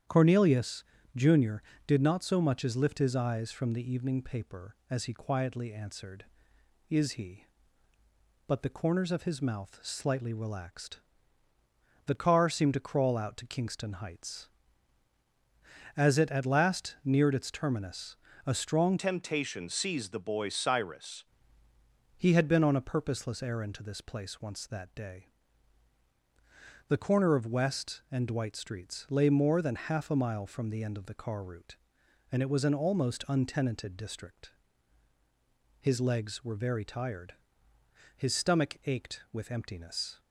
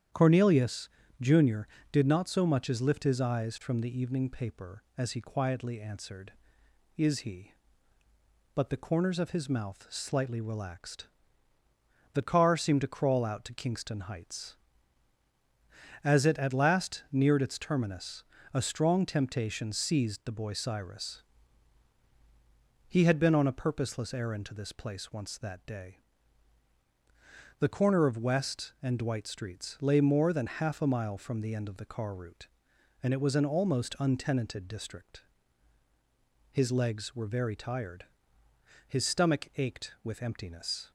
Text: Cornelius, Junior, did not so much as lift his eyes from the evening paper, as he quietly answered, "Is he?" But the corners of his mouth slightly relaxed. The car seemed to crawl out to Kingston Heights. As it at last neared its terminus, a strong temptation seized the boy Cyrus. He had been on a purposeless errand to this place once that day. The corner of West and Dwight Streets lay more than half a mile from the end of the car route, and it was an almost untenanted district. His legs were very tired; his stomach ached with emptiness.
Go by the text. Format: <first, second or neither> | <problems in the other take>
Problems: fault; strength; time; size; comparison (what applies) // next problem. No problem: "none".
second | starts louder than the rest; strong; until 1.3 s; 9 dB; strong in the second // changes voice from "temptation" to "Cyrus"; from 18.9 to 21.2 s; 2.3 s long